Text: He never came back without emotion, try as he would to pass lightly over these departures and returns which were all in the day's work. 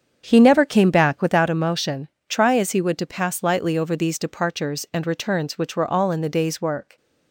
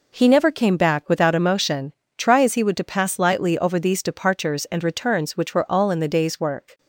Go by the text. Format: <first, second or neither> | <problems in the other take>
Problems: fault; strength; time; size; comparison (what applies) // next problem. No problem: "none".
second | starts louder than the rest; strong; until 1.4 s; 7.5 dB